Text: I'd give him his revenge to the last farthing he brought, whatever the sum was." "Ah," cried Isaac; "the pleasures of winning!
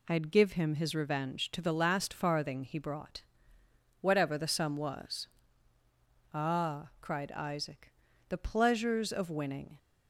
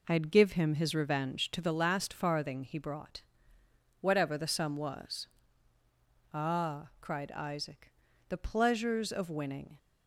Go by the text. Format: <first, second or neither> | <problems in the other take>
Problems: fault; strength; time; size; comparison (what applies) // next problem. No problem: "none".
first | starts louder than the rest; until 1.7 s; 4 dB